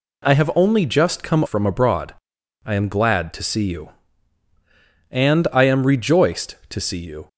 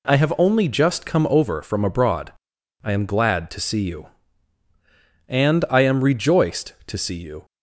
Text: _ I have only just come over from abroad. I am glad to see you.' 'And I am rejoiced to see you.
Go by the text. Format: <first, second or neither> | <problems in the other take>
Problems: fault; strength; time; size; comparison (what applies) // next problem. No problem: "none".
second | skips "over"; at 1.4 s